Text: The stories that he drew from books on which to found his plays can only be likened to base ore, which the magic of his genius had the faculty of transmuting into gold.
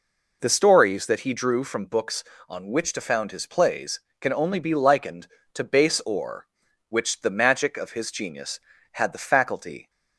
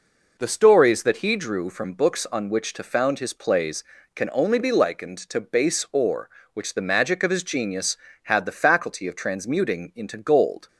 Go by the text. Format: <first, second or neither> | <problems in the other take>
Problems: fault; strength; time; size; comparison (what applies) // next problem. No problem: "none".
second | stops before "of transmuting into gold"; at 9.8 s